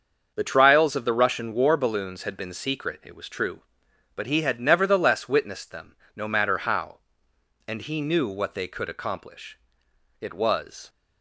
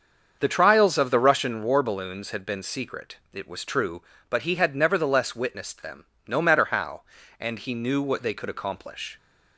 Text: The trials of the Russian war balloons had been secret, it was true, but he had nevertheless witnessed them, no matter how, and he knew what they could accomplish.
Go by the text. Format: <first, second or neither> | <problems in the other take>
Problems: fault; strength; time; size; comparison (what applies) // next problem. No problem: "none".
second | starts louder than the rest; until 1.3 s; 6.5 dB; also in the second // goes on to say "It was"; noticeable; from 10.2 s on; 0.68 s long